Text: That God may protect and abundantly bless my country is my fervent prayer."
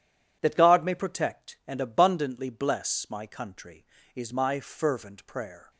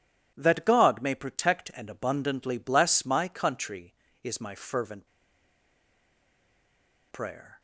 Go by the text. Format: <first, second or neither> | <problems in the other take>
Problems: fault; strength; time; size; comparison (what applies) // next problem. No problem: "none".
first | pauses between "fervent" and "prayer"; strong; at 5.0 s; 2.0 s long